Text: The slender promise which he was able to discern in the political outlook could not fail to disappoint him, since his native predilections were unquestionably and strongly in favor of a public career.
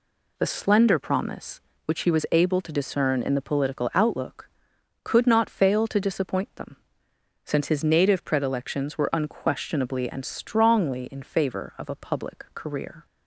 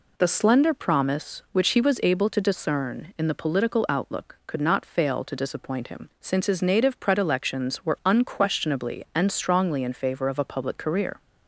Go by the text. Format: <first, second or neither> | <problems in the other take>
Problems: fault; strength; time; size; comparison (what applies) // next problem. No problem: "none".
second | says "them" for "him"; at 6.5 s